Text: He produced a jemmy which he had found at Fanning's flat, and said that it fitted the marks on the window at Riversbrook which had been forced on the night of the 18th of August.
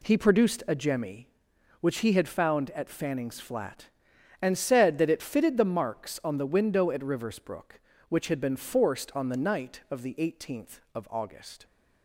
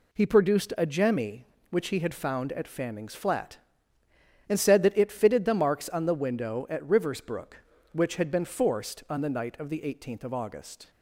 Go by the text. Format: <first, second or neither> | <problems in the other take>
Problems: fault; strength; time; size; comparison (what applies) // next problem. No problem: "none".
neither | none